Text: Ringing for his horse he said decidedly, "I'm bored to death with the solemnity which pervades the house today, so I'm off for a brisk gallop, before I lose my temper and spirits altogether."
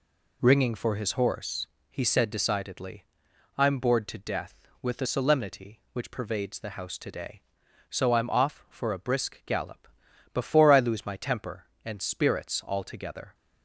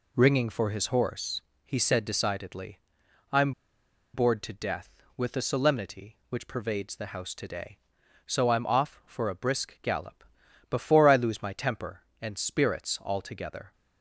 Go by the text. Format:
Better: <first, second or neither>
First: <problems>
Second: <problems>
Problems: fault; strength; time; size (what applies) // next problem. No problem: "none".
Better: first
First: pauses between "horse" and "he"; slight; at 1.6 s; 0.24 s long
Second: pauses between "horse" and "he"; slight; at 1.4 s; 0.24 s long // pauses between "I'm" and "bored"; noticeable; at 3.5 s; 0.62 s long